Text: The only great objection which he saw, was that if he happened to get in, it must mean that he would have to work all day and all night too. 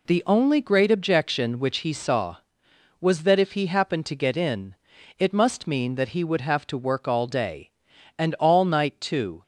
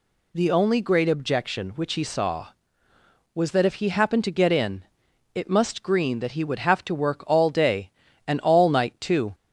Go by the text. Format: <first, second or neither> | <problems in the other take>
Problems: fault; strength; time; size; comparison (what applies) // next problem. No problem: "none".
first | says "green" for "mean"; at 5.8 s